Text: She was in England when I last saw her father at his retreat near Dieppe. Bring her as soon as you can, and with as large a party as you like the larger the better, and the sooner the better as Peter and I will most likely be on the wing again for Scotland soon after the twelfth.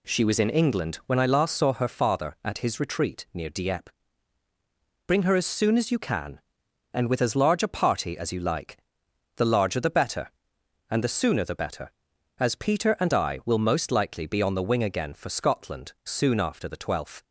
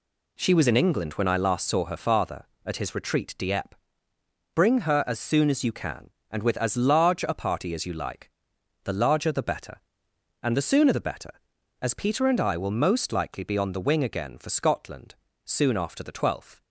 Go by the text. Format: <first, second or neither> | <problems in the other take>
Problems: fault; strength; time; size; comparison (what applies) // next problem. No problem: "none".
first | skips "near"; at 3.3 s // pauses between "like" and "the"; noticeable; at 8.3 s; 0.54 s long; noticeable in the first // pauses between "Scotland" and "soon"; slight; at 15.1 s; 0.30 s long